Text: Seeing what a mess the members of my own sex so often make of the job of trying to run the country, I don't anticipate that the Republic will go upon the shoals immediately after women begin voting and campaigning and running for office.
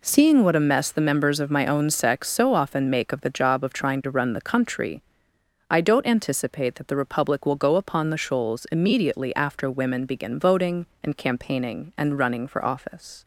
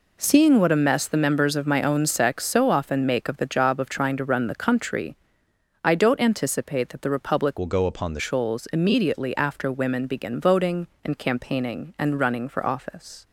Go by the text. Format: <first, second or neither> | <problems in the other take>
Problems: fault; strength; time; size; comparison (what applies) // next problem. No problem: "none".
first | changes voice from "will" to "the"; from 7.5 to 8.1 s; 0.6 s long